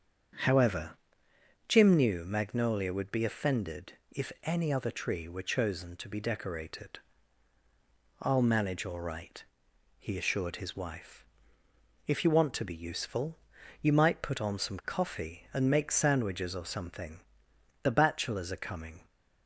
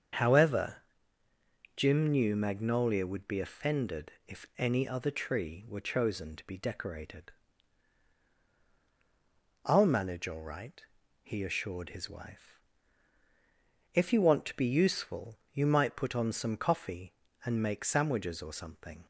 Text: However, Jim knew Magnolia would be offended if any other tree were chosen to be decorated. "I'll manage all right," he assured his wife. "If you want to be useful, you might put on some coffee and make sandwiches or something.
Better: second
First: starts louder than the rest; strong; until 2.1 s; 7.5 dB // pauses between "offended" and "if"; slight; at 3.9 s; 0.16 s long // goes on to say "The bachelors are coming"; noticeable; from 17.8 s on; 1.2 s long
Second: starts louder than the rest; until 2.1 s; 7 dB // pauses between "offended" and "if"; slight; at 4.1 s; 0.16 s long

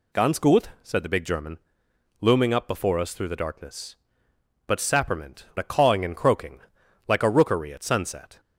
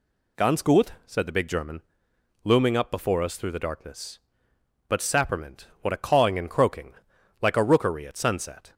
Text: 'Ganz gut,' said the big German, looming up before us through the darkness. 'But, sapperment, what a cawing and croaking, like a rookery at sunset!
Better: second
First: skips "what"; at 5.5 s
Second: none

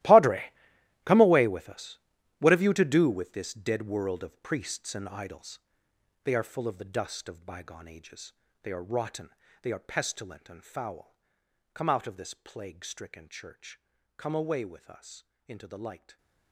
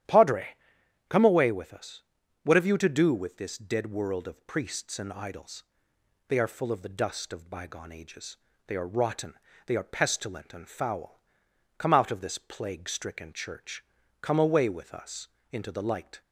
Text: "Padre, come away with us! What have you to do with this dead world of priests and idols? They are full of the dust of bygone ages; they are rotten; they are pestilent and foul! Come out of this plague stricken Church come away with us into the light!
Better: second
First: gets quieter; strong; throughout; 16 dB // starts louder than the rest; strong; until 1.5 s; 15.5 dB // pauses between "Church" and "come"; at 13.7 s; 0.38 s long // pauses between "us" and "into"; slight; at 15.2 s; 0.24 s long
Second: starts louder than the rest; strong; until 1.6 s; 11 dB // pauses between "Church" and "come"; at 13.8 s; 0.38 s long // pauses between "us" and "into"; slight; at 15.2 s; 0.24 s long

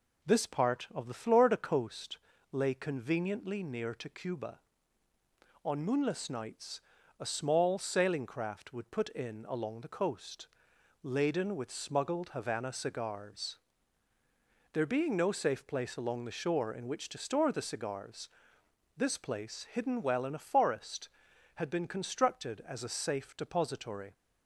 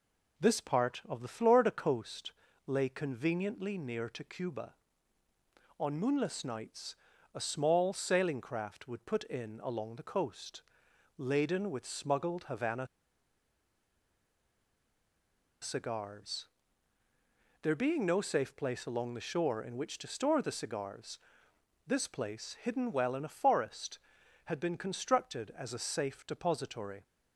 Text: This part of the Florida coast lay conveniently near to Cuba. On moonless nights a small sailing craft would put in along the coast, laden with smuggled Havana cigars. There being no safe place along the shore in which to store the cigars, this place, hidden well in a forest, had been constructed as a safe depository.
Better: first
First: pauses between "coast" and "lay"; slight; at 2.1 s; 0.33 s long // pauses between "nights" and "a"; at 6.7 s; 0.40 s long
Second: pauses between "coast" and "lay"; slight; at 2.3 s; 0.34 s long // pauses between "nights" and "a"; at 6.9 s; 0.40 s long // pauses between "Havana" and "cigars"; strong; at 12.8 s; 2.7 s long

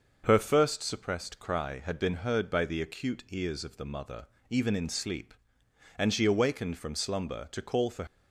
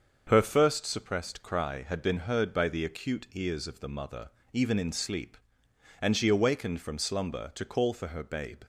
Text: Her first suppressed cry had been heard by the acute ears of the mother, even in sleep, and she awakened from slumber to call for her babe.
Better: second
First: starts louder than the rest; noticeable; until 1.2 s; 6 dB // stops before "her babe"; at 8.0 s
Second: starts louder than the rest; until 1.2 s; 6.5 dB

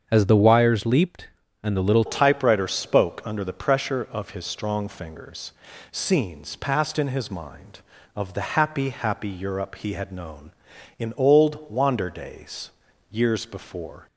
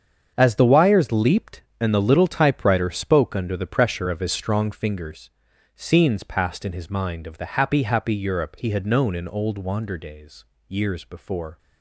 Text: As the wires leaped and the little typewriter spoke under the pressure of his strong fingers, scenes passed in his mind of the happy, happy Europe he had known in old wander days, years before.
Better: second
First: starts louder than the rest; until 1.0 s; 7 dB // changes voice at "typewriter"; from 2.0 s on; 12.0 s long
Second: starts louder than the rest; strong; until 1.3 s; 7 dB

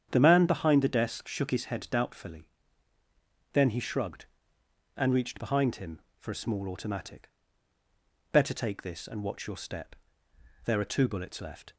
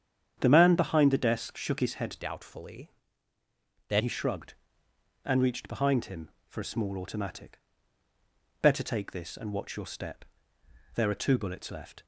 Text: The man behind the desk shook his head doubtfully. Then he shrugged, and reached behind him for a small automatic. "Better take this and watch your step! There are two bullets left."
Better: first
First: starts louder than the rest; strong; until 1.1 s; 8.5 dB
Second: starts louder than the rest; strong; until 1.4 s; 8.5 dB // changes voice from "doubtfully" to "Then"; from 2.2 to 4.0 s; 1.8 s long

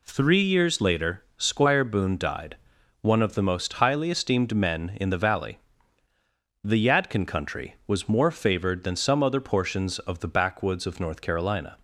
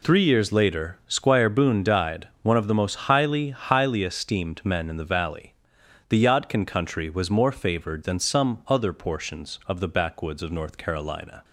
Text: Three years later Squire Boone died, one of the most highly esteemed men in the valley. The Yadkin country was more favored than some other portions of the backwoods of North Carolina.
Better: first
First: none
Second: says "highly" twice; at 3.4 s

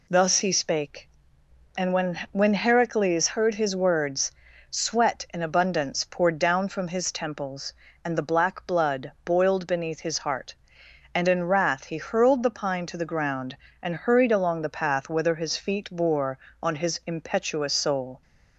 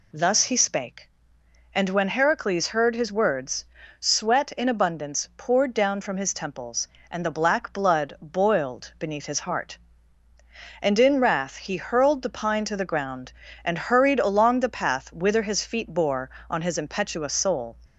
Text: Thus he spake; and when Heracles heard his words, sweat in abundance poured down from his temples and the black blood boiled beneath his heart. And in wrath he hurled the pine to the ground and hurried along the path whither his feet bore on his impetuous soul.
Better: second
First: says "when" twice; at 2.3 s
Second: none

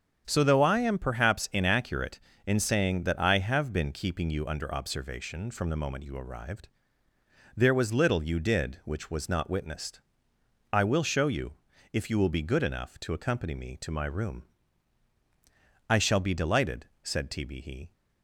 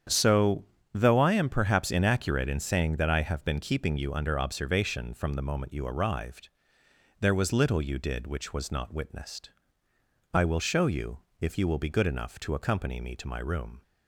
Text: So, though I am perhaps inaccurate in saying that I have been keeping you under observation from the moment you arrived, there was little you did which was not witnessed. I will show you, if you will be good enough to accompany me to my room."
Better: second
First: starts louder than the rest; strong; until 1.2 s; 7.5 dB // goes on to say "I shall be delighted said T B He"; strong; from 15.8 s on; 2.0 s long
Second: starts louder than the rest; strong; until 1.3 s; 8.5 dB

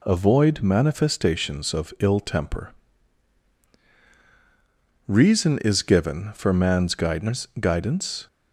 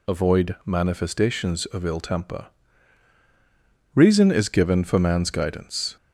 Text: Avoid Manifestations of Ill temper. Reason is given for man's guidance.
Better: second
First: says "guidance" twice; at 7.6 s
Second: none

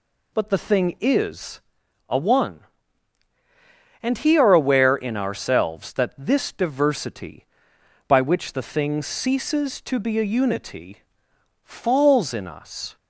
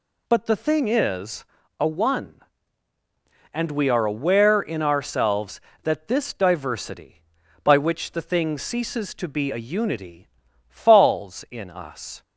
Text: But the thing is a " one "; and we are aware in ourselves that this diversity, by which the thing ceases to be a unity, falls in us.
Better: second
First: pauses between "is" and "a"; noticeable; at 1.5 s; 0.50 s long // says "he" for "we"; at 4.1 s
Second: pauses between "is" and "a"; slight; at 1.4 s; 0.34 s long

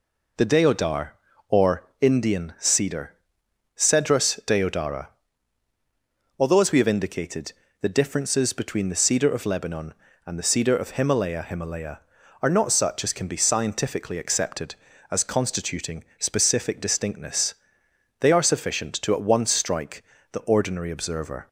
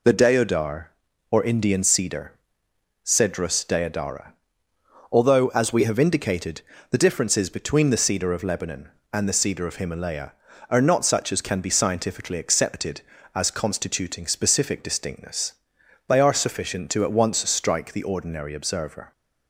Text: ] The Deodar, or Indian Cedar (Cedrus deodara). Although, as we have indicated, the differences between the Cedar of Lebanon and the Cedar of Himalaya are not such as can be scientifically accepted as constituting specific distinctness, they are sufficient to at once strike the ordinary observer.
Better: second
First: pauses between "or" and "Indian"; slight; at 1.8 s; 0.16 s long // says "Himalaya" twice; at 11.4 s // pauses between "constituting" and "specific"; slight; at 16.0 s; 0.16 s long // pauses between "strike" and "the"; slight; at 20.0 s; 0.30 s long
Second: none

